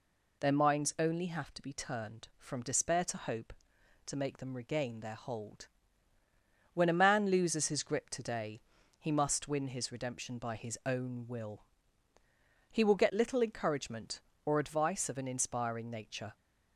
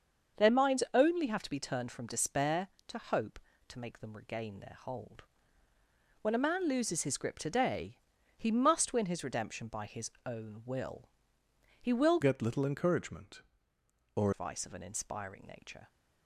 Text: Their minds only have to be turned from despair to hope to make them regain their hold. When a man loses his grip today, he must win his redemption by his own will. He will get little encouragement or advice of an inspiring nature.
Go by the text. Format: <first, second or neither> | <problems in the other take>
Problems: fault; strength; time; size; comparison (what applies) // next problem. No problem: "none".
first | starts louder than the rest; until 1.4 s; 6.5 dB // changes voice from "get" to "or"; from 12.2 to 14.3 s; 2.1 s long